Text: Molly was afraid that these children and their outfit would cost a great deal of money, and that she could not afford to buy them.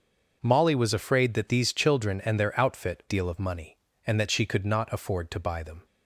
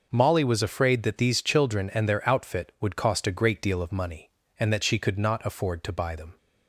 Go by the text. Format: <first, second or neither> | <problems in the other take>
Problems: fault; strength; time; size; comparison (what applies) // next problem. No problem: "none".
second | starts louder than the rest; noticeable; until 1.4 s; 6 dB // skips "would cost a great"; at 3.0 s